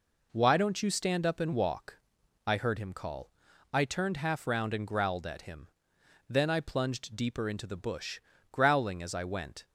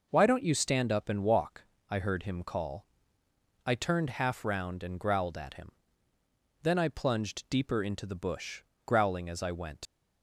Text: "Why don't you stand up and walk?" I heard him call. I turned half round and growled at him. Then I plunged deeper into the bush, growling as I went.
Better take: first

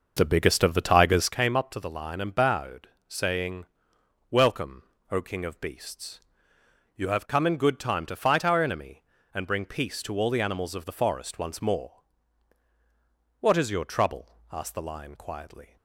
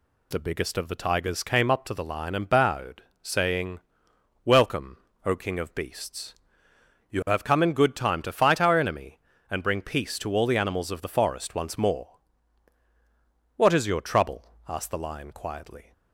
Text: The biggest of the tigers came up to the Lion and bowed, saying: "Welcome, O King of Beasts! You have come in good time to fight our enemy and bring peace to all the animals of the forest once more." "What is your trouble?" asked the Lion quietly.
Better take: second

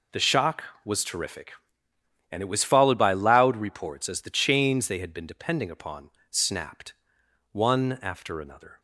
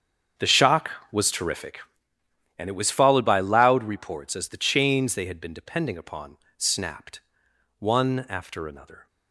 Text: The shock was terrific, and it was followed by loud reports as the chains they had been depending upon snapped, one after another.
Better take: first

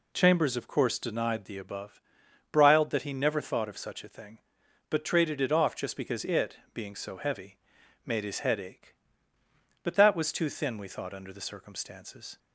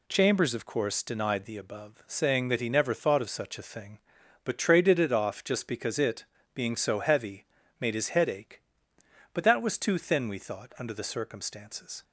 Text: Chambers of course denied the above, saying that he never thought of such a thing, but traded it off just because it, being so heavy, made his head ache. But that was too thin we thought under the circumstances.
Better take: second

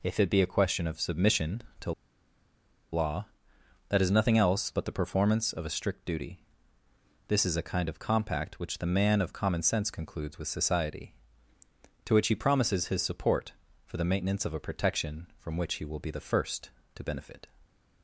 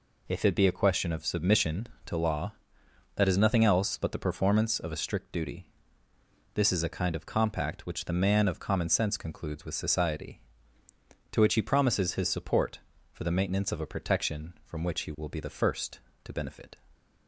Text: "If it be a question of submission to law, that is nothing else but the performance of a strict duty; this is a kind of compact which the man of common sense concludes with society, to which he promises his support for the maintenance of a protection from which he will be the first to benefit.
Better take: second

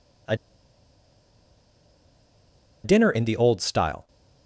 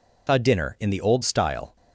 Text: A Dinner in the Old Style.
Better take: second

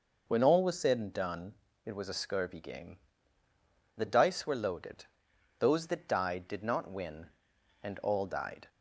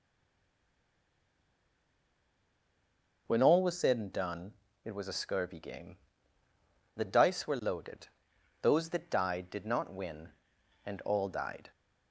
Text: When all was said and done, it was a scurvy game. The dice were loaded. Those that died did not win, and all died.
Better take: first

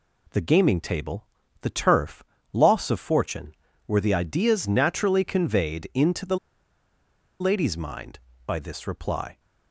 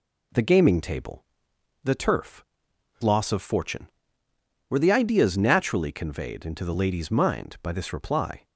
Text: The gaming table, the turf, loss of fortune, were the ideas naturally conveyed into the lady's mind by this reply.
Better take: second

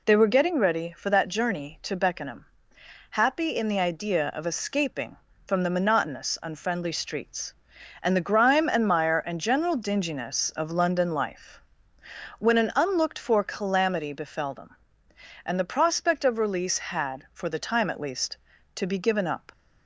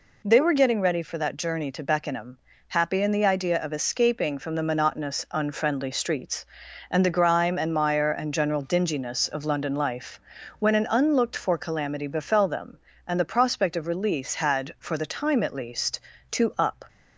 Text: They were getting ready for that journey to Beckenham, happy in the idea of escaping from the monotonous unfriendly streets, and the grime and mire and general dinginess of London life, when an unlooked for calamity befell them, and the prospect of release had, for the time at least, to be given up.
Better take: first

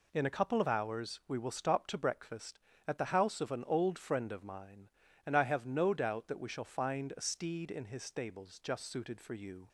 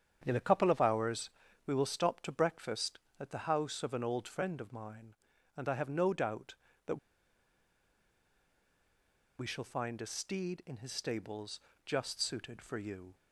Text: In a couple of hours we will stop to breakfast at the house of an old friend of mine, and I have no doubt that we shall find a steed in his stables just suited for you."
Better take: first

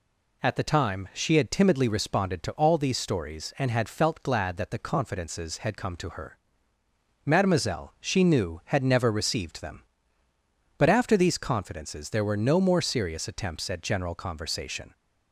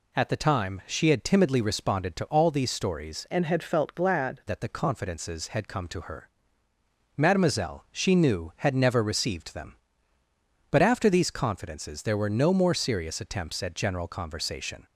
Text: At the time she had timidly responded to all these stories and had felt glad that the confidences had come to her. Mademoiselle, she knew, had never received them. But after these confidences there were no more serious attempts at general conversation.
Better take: first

